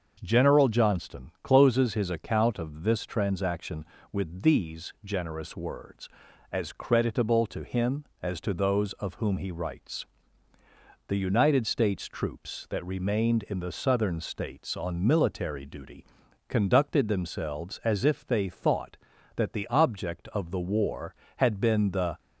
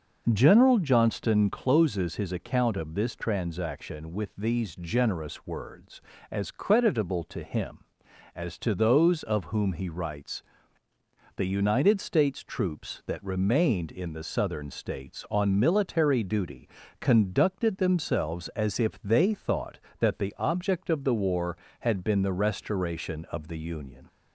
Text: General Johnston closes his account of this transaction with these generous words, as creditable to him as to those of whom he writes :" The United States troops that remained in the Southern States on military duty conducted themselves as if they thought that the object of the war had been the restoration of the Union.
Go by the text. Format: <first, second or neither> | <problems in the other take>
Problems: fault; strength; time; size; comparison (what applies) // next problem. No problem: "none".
second | starts louder than the rest; until 1.2 s; 6.5 dB // pauses between "duty" and "conducted"; at 16.0 s; 0.44 s long; slight in the second // stops before "restoration of the Union"; at 22.1 s